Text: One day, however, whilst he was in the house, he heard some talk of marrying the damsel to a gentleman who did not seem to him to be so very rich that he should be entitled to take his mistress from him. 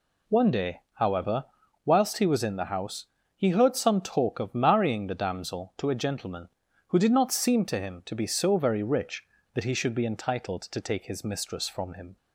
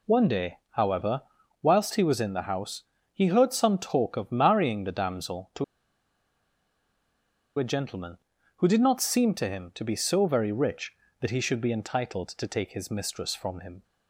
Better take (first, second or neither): first